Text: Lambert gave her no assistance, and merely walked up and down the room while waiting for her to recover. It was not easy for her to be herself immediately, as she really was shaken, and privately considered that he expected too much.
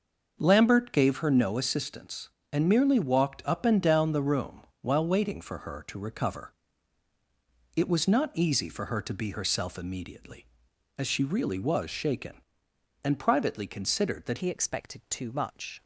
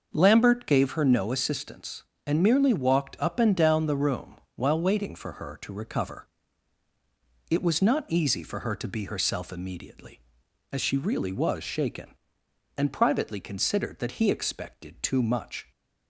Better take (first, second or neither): second